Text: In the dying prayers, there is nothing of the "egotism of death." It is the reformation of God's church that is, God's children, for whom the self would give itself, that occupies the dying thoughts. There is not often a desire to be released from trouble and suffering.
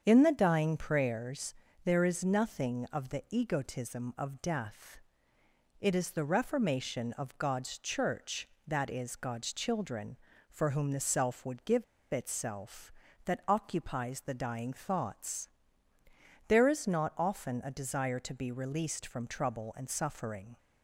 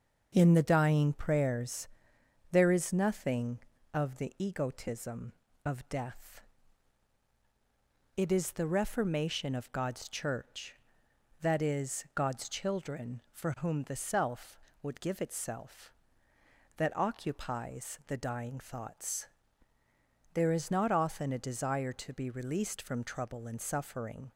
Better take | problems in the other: second | starts louder than the rest; strong; until 1.0 s; 7.5 dB; also in the second // pauses between "give" and "itself"; slight; at 11.8 s; 0.28 s long

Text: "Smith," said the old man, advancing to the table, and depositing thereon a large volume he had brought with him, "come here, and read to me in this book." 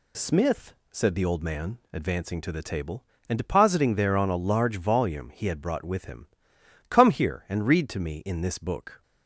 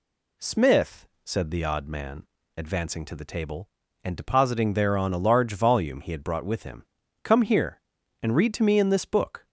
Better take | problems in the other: first | says "odd" for "old"; at 1.6 s

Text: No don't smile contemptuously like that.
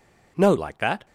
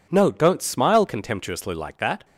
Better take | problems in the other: second | skips "don't smile contemptuously"; at 0.5 s

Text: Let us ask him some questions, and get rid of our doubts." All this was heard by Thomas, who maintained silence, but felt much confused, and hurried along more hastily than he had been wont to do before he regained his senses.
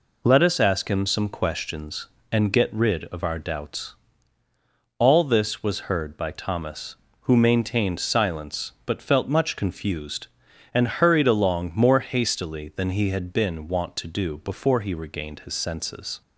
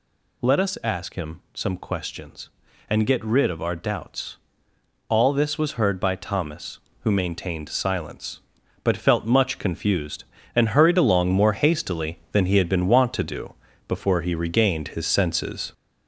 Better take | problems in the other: first | gets louder; noticeable; throughout; 5 dB // pauses between "do" and "before"; slight; at 13.5 s; 0.34 s long

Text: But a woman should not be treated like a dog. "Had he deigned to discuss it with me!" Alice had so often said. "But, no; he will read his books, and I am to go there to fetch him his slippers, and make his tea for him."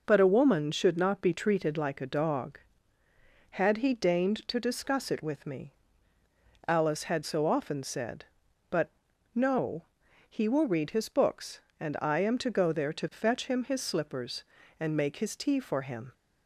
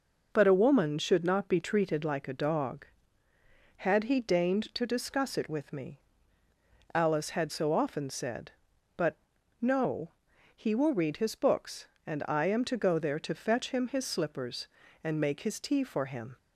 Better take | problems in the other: neither | none

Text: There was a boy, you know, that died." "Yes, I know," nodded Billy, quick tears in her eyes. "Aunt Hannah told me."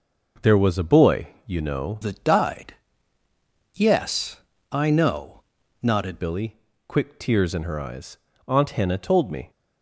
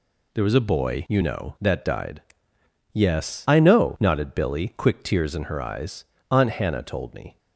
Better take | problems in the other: second | changes voice from "that" to "nodded"; from 2.0 to 6.1 s; 4.1 s long

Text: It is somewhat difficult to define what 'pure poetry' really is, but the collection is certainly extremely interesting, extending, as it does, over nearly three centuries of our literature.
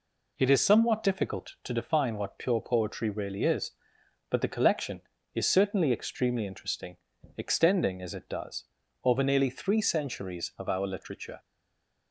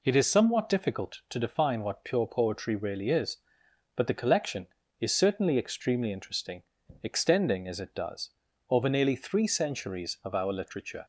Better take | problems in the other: second | stays silent after the last word; slight; from 11.3 s on; 0.8 s long

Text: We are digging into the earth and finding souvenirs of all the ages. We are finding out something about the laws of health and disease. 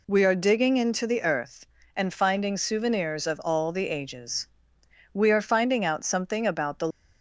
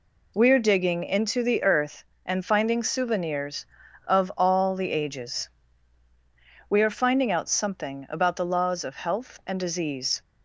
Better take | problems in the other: second | stops before "laws of health and disease"; at 6.9 s

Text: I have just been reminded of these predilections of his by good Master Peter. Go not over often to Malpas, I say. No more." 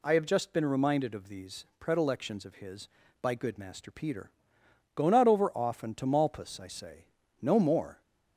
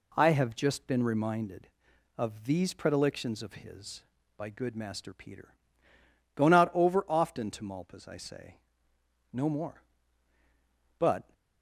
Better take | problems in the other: first | goes on to say "But"; slight; from 10.9 s on; 0.34 s long

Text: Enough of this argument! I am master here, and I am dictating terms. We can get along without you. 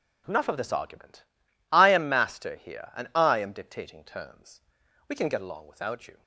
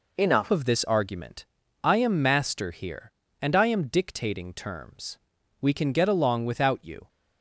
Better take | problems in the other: first | changes voice at "of"; from 0.5 s on; 6.5 s long

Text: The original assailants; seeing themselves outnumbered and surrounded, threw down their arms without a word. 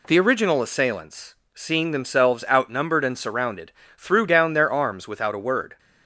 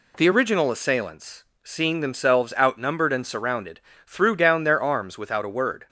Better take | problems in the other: neither | none

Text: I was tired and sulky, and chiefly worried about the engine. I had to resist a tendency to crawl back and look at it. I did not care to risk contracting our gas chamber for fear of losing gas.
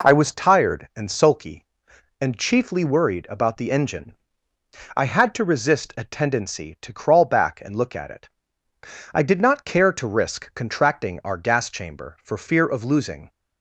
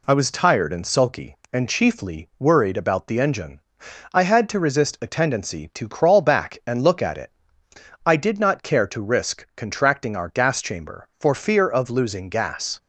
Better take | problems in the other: second | stops before "gas"; at 13.2 s

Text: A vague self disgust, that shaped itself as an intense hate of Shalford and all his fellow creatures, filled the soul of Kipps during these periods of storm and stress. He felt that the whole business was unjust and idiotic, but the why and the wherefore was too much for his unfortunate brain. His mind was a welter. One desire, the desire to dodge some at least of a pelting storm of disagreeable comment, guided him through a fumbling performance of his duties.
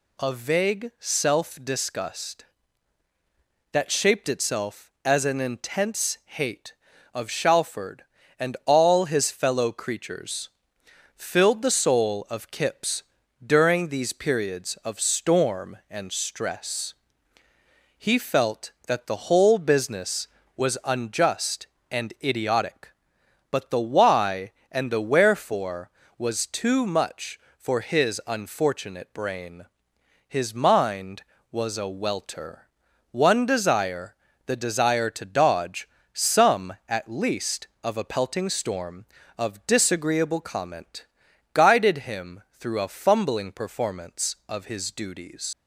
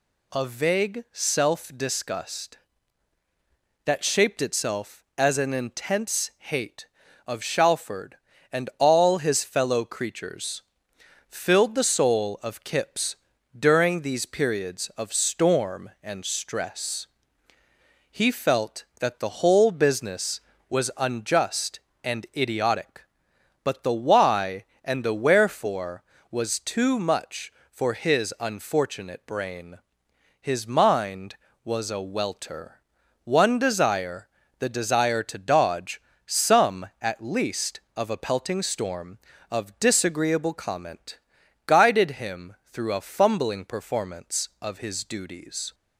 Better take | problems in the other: second | pauses between "Kipps" and "during"; at 13.0 s; 0.42 s long; also in the second // pauses between "dodge" and "some"; slight; at 35.8 s; 0.24 s long; slight in the second // pauses between "him" and "through"; slight; at 42.4 s; 0.18 s long; slight in the second // leaves "duties" unfinished; at 45.5 s; 80 ms

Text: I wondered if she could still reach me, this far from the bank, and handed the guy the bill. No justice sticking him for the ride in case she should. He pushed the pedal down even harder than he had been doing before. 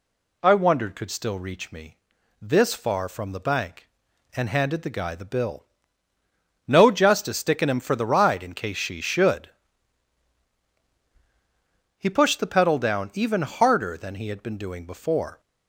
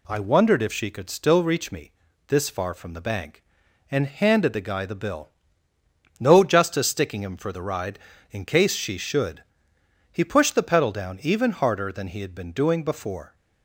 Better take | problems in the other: second | skips "if she"; at 0.9 s

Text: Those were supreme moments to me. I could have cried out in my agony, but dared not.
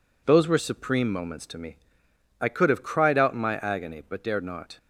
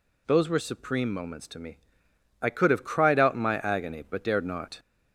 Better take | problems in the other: first | gets louder; slight; throughout; 2.5 dB

